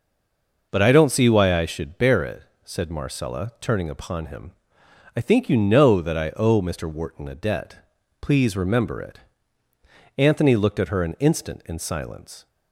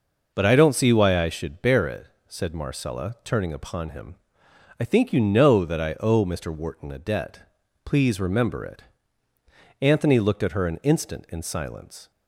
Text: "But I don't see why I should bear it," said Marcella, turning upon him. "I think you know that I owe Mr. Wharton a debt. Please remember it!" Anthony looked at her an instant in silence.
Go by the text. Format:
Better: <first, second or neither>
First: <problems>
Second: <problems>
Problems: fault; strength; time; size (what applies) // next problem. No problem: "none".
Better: second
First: stays silent before the first word; slight; until 0.7 s; 0.7 s long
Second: none